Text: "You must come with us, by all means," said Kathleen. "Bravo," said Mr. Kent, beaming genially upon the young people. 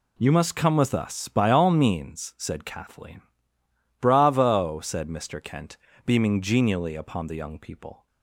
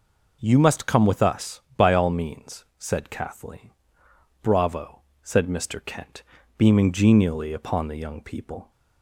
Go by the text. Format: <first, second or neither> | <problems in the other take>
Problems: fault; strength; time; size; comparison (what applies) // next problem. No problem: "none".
neither | none